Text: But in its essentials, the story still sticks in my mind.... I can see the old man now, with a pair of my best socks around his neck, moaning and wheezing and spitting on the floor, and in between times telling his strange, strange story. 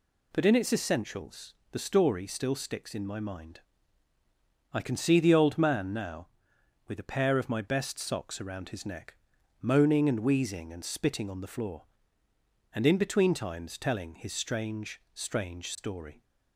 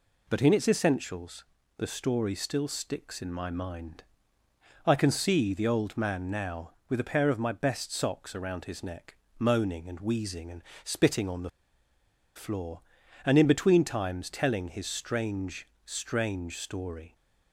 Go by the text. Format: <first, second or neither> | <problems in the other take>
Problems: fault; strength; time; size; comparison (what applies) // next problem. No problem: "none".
first | pauses between "and" and "spitting"; slight; at 10.6 s; 0.22 s long // pauses between "the" and "floor"; noticeable; at 11.4 s; 0.86 s long